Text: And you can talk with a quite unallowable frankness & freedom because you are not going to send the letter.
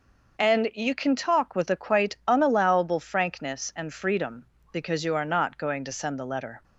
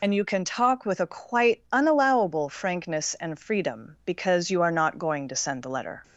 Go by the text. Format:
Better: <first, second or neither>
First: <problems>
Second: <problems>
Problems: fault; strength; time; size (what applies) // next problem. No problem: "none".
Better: first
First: none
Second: loses the start of "And"; at 0.0 s; 40 ms